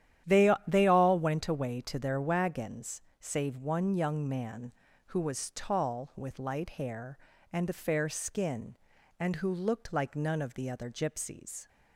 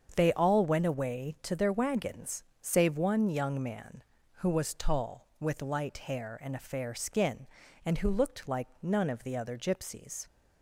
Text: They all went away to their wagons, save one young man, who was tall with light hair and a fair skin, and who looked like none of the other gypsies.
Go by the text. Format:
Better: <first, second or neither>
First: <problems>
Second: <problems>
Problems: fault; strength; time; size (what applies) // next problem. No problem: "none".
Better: second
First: starts louder than the rest; strong; until 1.4 s; 10.5 dB // says "They" twice; at 0.6 s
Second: starts louder than the rest; strong; until 1.1 s; 7.5 dB